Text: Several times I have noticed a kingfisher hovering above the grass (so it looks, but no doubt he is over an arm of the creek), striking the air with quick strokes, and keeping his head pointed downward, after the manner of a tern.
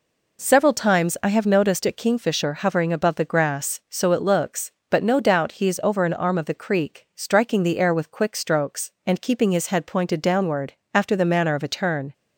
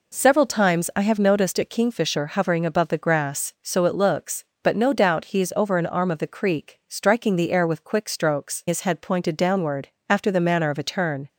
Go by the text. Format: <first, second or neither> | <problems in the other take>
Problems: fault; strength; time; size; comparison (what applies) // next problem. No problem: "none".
first | skips "and keeping"; at 8.6 s